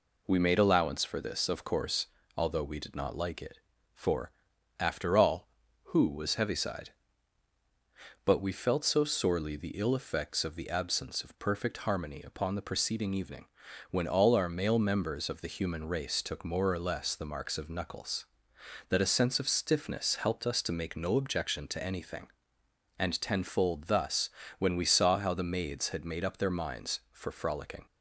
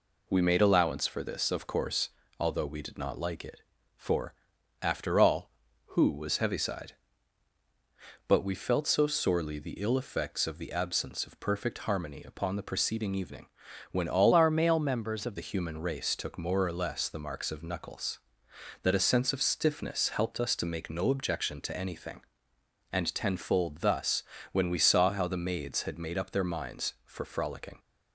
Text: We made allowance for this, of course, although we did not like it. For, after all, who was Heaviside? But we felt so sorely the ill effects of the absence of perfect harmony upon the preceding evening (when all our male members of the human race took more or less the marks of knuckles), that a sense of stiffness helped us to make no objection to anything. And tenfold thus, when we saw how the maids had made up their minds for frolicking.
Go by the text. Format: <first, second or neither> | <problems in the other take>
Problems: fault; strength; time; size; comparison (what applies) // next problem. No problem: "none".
first | changes voice from "our" to "of"; from 14.3 to 15.3 s; 1.0 s long